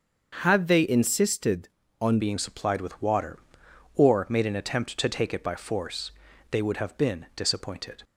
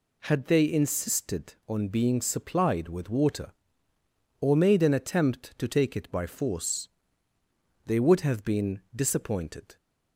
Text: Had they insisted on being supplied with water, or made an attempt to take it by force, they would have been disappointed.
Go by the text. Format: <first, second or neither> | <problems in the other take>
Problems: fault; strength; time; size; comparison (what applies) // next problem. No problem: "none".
second | starts louder than the rest; until 1.4 s; 6.5 dB // changes voice at "being"; from 2.1 s on; 5.9 s long